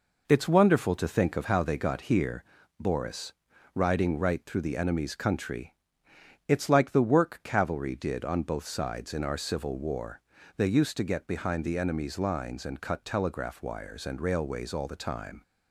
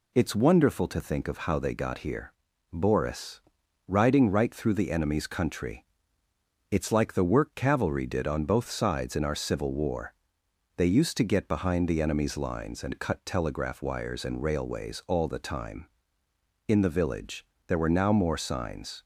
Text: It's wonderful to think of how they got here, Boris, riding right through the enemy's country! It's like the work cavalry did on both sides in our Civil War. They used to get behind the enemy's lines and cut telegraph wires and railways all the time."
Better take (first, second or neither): first